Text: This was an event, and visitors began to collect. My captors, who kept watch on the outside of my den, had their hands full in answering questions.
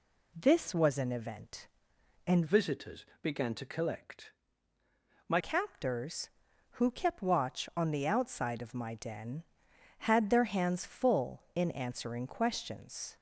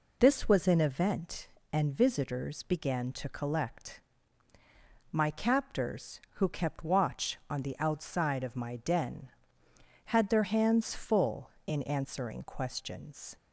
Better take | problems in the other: second | changes voice from "visitors" to "My"; from 2.4 to 5.3 s; 2.9 s long // pauses between "visitors" and "began"; slight; at 3.0 s; 0.16 s long

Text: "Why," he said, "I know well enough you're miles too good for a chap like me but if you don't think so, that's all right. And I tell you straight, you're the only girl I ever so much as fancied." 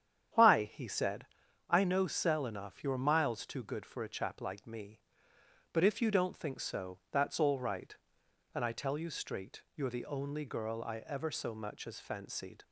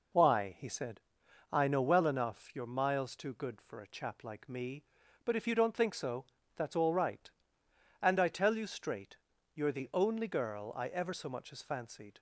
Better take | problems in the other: second | starts louder than the rest; strong; until 1.7 s; 9.5 dB // says "cell" for "well"; at 2.0 s

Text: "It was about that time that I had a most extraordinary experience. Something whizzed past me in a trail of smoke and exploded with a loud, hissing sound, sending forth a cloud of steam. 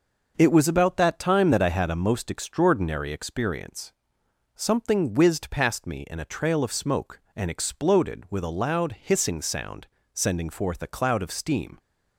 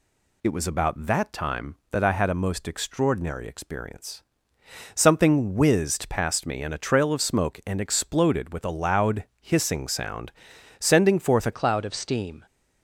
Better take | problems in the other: first | changes voice at "cloud"; from 11.5 s on; 0.9 s long

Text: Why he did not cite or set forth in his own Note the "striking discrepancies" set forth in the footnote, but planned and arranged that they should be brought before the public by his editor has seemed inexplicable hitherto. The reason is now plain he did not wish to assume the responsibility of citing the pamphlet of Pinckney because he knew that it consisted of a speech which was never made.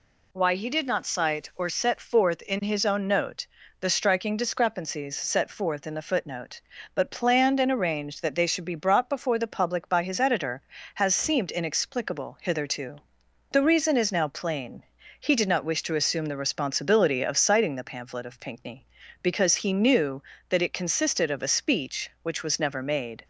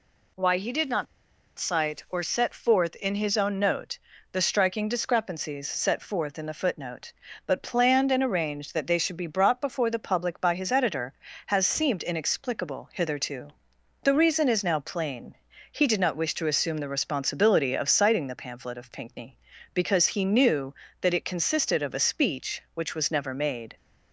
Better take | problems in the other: first | pauses between "not" and "cite"; noticeable; at 1.0 s; 0.53 s long // pauses between "Note" and "the"; slight; at 3.9 s; 0.36 s long; slight in the first // pauses between "plain" and "he"; at 15.3 s; 0.38 s long; also in the first

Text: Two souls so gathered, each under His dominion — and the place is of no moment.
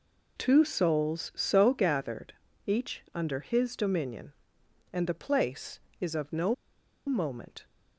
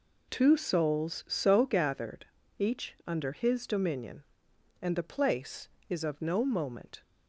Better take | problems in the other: second | pauses between "no" and "moment"; noticeable; at 6.5 s; 0.52 s long

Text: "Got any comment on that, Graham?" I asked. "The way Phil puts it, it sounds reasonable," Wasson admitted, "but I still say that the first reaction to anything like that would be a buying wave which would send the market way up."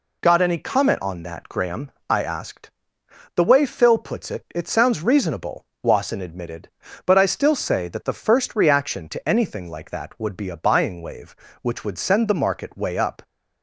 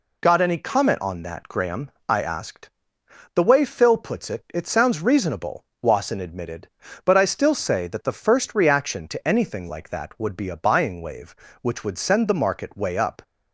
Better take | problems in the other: neither | none

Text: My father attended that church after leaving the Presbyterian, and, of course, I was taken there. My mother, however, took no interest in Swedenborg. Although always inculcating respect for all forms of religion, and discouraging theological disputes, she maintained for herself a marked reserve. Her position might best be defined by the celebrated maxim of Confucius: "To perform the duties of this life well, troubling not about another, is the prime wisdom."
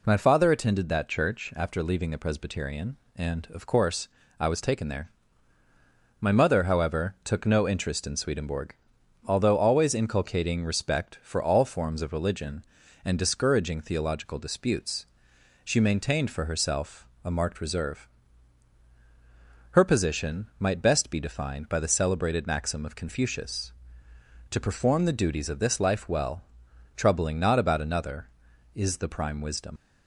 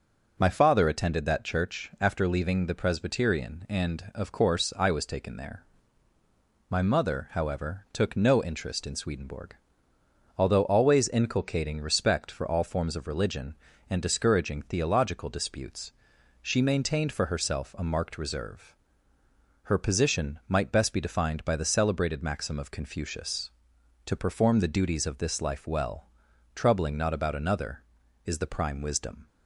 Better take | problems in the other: second | pauses between "herself" and "a"; slight; at 17.0 s; 0.16 s long // leaves "wisdom" unfinished; at 29.7 s; 70 ms

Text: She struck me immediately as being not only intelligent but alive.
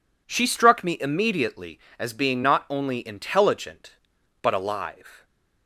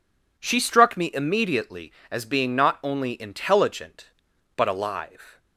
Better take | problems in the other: neither | none

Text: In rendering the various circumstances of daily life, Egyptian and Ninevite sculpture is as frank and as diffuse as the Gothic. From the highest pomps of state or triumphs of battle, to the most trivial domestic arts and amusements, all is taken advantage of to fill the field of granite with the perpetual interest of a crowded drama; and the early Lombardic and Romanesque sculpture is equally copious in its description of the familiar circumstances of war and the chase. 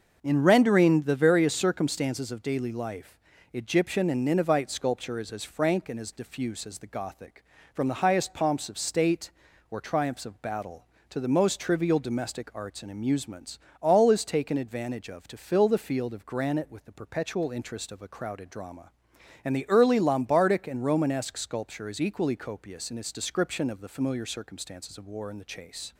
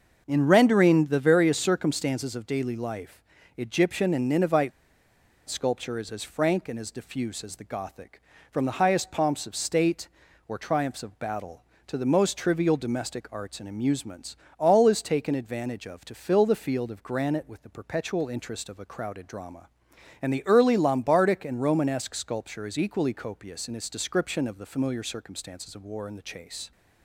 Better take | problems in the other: first | starts louder than the rest; until 1.2 s; 6 dB; also in the first // pauses between "Ninevite" and "sculpture"; noticeable; at 4.7 s; 0.78 s long

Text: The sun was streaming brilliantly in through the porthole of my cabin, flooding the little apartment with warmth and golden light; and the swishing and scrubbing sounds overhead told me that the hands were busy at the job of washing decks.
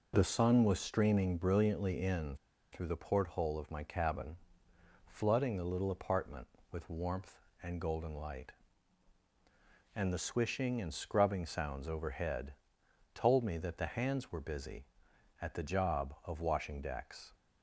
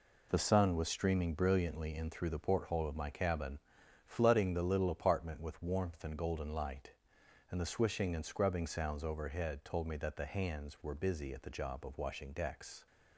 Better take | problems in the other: second | pauses between "in" and "through"; slight; at 2.3 s; 0.35 s long // pauses between "overhead" and "told"; noticeable; at 12.5 s; 0.58 s long

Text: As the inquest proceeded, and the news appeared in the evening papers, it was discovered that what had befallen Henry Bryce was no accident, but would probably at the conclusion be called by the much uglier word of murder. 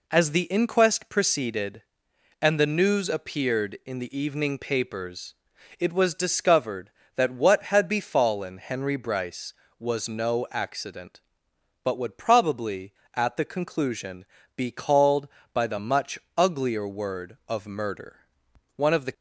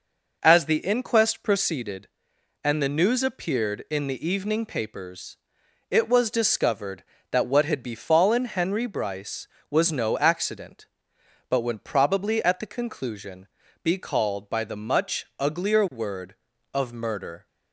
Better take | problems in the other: second | pauses between "conclusion" and "be"; slight; at 14.2 s; 0.32 s long; slight in the second // pauses between "much" and "uglier"; slight; at 16.1 s; 0.18 s long // goes on to say "One of the"; slight; from 18.7 s on; 0.38 s long

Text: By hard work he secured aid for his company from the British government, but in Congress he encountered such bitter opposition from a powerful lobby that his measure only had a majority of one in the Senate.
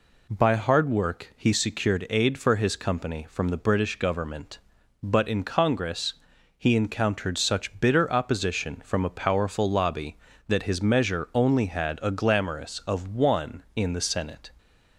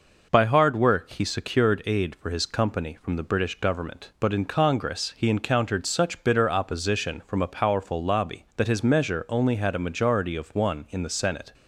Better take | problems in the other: second | pauses between "Congress" and "he"; at 6.1 s; 0.44 s long // says "glamorous" for "majority"; at 12.0 s

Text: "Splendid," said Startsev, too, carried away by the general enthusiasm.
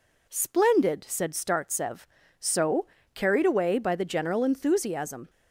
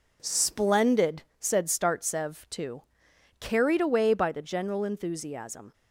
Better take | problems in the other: second | says "so" for "too"; at 2.3 s

